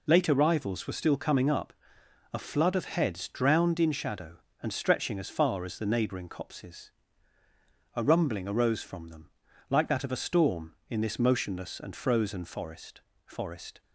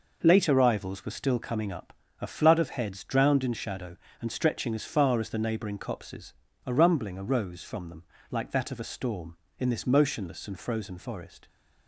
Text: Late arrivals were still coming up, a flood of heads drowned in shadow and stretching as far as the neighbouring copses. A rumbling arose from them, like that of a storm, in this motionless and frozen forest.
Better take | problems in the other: second | says "forest" twice; at 13.2 s

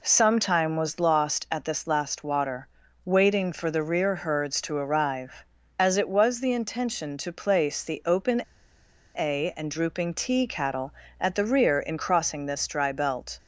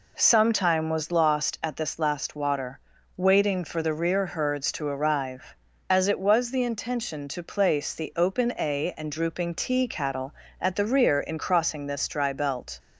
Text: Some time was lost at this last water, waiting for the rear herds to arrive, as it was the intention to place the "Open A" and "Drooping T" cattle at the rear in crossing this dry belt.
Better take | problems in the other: second | pauses between "Open" and "A"; noticeable; at 8.4 s; 0.76 s long

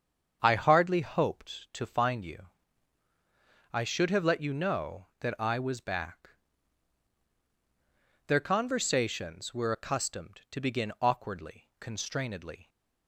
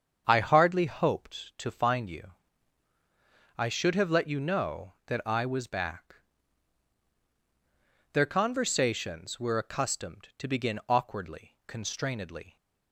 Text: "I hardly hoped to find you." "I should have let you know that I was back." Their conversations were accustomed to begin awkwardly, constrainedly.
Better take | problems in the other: neither | starts louder than the rest; strong; the same in both

